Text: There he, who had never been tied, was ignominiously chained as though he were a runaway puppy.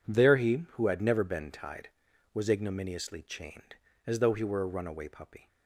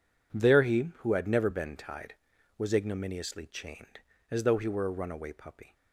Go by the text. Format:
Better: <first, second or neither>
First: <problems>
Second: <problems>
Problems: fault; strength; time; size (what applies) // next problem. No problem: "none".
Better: neither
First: none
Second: none